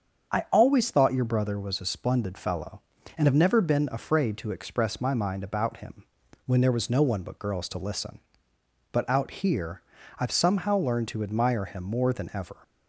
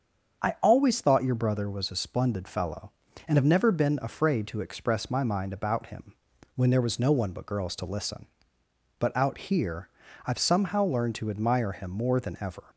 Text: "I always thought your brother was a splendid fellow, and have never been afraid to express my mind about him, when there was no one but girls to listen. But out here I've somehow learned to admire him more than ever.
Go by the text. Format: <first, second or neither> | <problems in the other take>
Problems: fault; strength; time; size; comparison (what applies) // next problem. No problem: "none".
neither | starts louder than the rest; strong; the same in both // pauses between "here" and "I've"; the same in both